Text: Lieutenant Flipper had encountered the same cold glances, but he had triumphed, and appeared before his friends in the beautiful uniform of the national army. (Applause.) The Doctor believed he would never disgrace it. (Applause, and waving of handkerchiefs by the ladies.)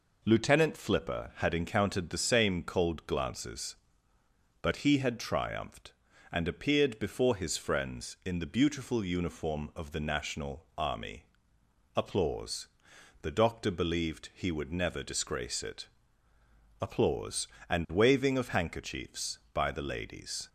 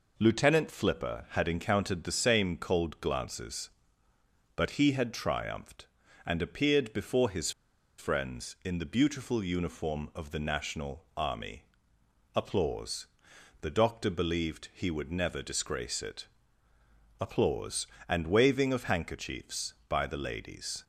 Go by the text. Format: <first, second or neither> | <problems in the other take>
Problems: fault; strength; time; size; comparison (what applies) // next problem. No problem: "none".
first | pauses between "his" and "friends"; noticeable; at 7.4 s; 0.48 s long